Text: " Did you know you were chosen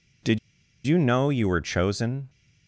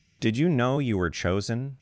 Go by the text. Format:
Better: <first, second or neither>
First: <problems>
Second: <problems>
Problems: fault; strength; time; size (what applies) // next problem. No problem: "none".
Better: second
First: pauses between "Did" and "you"; noticeable; at 0.3 s; 0.46 s long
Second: none